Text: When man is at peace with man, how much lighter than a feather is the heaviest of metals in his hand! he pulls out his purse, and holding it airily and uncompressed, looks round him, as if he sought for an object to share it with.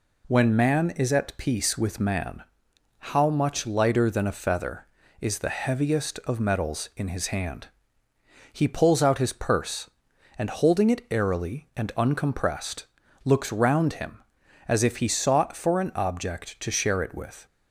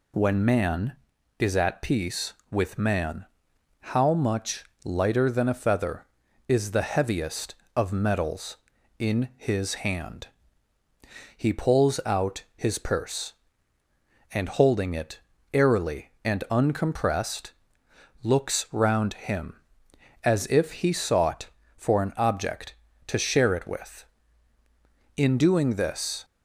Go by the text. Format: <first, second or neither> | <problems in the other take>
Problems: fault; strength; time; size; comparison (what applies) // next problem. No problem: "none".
first | pauses between "much" and "lighter"; slight; at 4.6 s; 0.22 s long // pauses between "it" and "airily"; slight; at 15.1 s; 0.34 s long // goes on to say "In doing this"; noticeable; from 25.1 s on; 1.0 s long